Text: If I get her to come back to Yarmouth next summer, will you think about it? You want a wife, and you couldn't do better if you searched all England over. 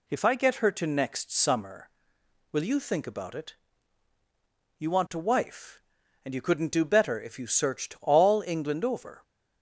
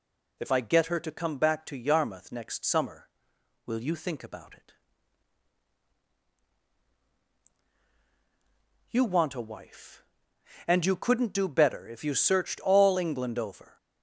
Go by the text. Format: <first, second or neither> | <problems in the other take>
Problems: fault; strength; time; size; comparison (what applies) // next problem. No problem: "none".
second | skips "come back to Yarmouth"; at 0.8 s